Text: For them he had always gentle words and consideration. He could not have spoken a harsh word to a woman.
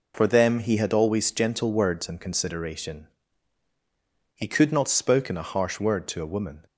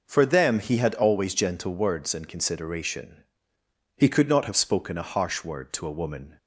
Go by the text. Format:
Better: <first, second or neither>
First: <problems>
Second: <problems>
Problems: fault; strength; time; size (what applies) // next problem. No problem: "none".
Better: second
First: skips "have"; at 4.8 s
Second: none